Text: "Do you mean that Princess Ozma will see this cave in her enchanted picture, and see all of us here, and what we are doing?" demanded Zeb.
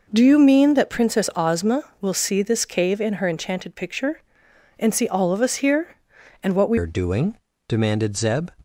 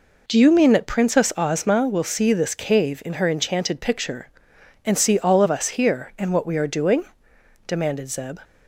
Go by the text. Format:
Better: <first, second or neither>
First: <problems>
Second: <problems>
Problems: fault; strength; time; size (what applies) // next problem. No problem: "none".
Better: second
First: changes voice at "are"; from 6.7 s on; 1.8 s long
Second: none